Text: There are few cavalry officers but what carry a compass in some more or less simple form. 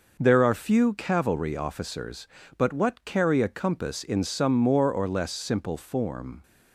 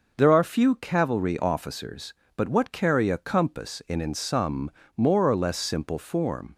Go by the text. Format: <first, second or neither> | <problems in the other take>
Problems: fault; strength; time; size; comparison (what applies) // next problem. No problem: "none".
first | says "in" twice; at 3.9 s // pauses between "some" and "more"; slight; at 4.6 s; 0.26 s long